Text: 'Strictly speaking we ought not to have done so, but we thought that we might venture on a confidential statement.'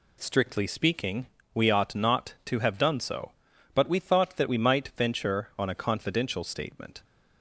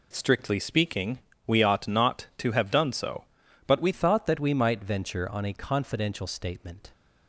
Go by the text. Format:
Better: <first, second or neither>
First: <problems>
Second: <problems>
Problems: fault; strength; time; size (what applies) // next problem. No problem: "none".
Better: first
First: pauses between "speaking" and "we"; slight; at 1.2 s; 0.26 s long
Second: pauses between "speaking" and "we"; slight; at 1.1 s; 0.26 s long // changes voice at "thought"; from 3.9 s on; 3.0 s long